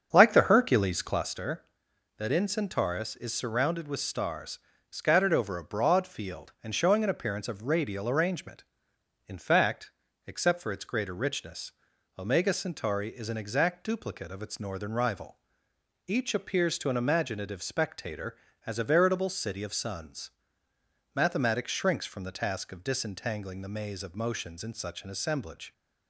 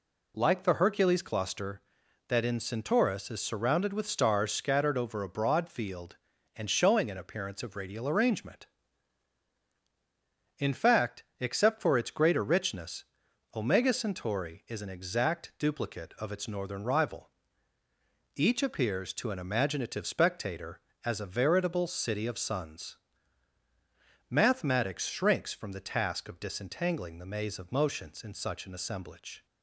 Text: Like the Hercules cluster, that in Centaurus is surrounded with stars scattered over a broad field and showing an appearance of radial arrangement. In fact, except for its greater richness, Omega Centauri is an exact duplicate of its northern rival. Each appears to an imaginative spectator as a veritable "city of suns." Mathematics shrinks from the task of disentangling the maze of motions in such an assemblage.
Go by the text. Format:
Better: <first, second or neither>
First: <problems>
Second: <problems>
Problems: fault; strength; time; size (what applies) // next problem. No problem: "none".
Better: second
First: starts louder than the rest; until 1.4 s; 7 dB // pauses between "stars" and "scattered"; slight; at 4.5 s; 0.32 s long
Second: none